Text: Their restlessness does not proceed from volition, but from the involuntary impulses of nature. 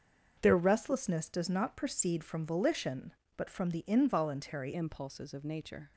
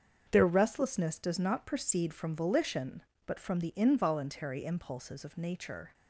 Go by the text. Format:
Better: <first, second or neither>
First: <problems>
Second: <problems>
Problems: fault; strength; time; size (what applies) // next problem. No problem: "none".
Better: second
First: starts louder than the rest; until 1.4 s; 6.5 dB // changes voice at "impulses"; from 4.7 s on; 1.2 s long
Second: starts louder than the rest; until 1.3 s; 7 dB